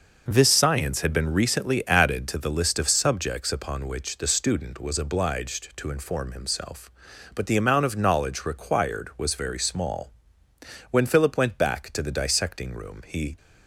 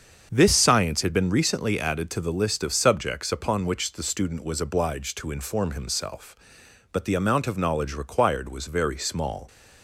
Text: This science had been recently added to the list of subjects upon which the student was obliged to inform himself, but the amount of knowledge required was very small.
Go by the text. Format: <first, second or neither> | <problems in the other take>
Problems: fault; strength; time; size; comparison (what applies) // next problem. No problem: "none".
second | starts louder than the rest; noticeable; until 1.2 s; 6 dB; also in the second // goes on to say "When Philip went back to the dissecting room he"; strong; from 10.9 s on; 2.4 s long